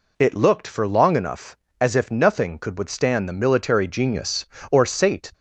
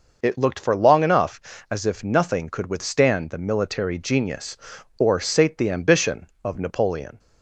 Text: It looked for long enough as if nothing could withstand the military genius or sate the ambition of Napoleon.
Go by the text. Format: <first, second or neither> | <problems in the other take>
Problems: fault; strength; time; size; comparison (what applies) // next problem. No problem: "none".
second | stops before "the ambition of Napoleon"; at 5.3 s